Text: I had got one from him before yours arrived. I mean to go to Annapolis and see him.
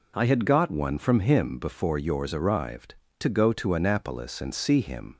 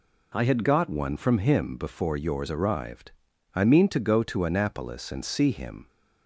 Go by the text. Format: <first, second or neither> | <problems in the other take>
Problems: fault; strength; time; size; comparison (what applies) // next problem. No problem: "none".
second | skips "I mean"; at 3.0 s